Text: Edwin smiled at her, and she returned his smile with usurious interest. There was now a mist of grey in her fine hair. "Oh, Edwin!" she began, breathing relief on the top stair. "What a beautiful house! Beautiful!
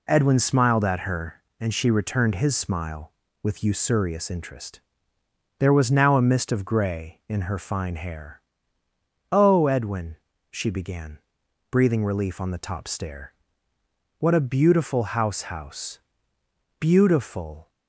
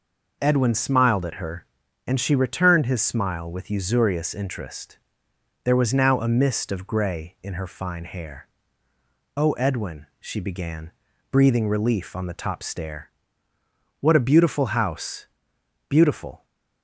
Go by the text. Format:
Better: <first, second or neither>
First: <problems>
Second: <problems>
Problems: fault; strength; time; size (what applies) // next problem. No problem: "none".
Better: second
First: says "house" twice; at 15.4 s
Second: none